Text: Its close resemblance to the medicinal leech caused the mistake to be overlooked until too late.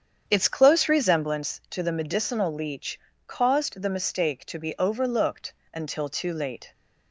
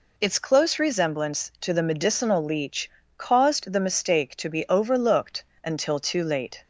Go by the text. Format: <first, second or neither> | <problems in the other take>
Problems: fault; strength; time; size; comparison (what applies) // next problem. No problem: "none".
second | starts louder than the rest; strong; until 1.5 s; 8 dB // pauses between "leech" and "caused"; slight; at 2.9 s; 0.30 s long; slight in the second // pauses between "overlooked" and "until"; slight; at 5.5 s; 0.18 s long; slight in the second